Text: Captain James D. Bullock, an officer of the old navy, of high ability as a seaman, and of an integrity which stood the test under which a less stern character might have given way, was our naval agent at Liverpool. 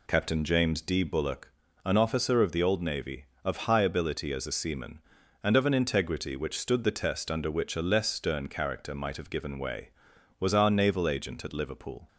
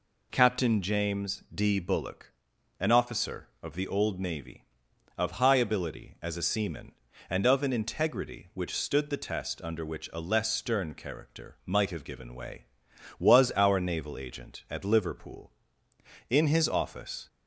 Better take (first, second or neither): first